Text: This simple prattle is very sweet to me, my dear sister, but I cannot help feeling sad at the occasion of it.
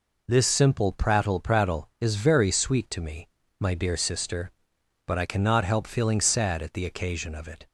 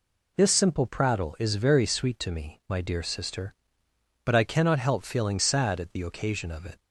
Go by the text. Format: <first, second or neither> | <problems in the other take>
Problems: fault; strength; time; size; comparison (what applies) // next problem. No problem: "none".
second | says "prattle" twice; at 1.3 s